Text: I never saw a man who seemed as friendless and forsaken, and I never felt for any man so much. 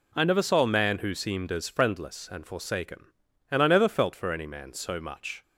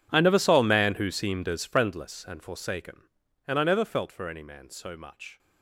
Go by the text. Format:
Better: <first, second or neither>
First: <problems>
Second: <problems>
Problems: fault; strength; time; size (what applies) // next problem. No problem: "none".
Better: first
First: none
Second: gets quieter; strong; throughout; 20.5 dB